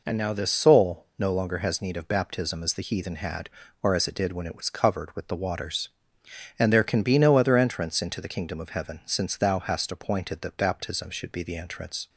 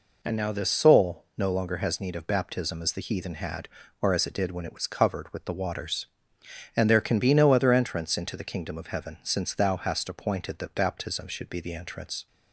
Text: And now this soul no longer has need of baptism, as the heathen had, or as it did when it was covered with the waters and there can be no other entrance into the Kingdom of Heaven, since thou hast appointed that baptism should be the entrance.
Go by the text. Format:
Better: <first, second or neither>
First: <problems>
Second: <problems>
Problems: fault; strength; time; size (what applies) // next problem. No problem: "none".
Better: neither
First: none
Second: none